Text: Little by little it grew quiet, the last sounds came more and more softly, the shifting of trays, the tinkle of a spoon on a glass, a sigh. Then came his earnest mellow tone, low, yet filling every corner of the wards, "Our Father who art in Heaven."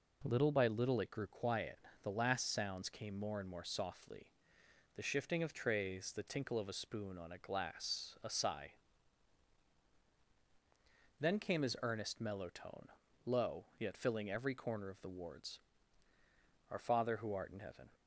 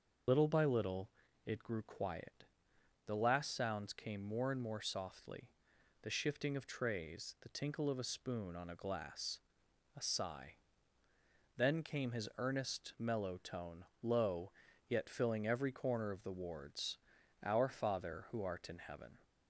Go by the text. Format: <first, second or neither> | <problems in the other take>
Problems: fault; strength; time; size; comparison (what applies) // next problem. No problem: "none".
first | loses the start of "Little"; at 0.2 s; 65 ms // starts louder than the rest; until 1.6 s; 6 dB // pauses between "little" and "it"; slight; at 1.0 s; 0.36 s long